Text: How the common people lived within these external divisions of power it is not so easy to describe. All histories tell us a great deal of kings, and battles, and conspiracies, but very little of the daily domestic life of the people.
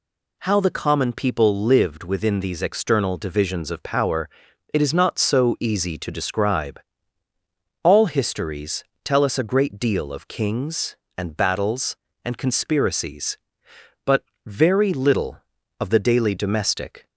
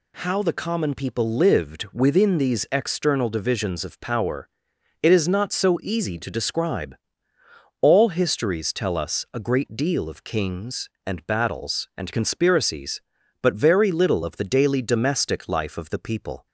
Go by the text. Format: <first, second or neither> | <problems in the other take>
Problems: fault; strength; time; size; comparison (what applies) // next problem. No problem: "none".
second | pauses between "power" and "it"; at 4.2 s; 0.44 s long; noticeable in the second // pauses between "histories" and "tell"; slight; at 8.8 s; 0.22 s long // pauses between "but" and "very"; slight; at 14.2 s; 0.22 s long // stops before "life of the people"; at 17.0 s